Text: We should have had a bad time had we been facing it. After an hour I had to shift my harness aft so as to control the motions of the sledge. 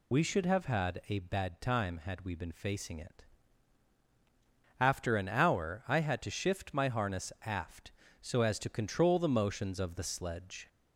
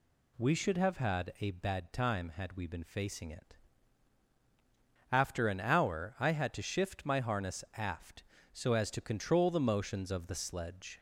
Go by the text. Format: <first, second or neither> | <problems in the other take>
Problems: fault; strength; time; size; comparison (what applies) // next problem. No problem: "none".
second | loses the start of "We"; at 0.1 s; 70 ms